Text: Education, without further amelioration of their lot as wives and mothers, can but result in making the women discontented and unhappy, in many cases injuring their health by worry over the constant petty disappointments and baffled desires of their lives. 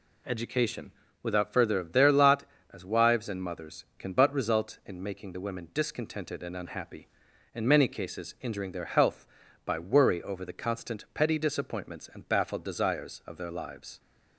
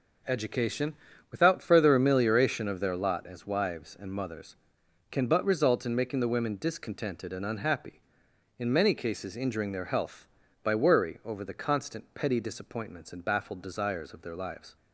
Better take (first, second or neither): second